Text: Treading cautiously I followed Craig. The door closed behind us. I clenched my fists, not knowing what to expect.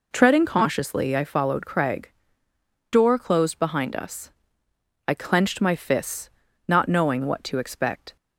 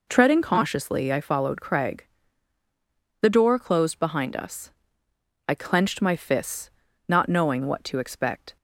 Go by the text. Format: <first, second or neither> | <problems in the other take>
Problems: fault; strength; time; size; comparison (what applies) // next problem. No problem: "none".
second | skips "The"; at 2.5 s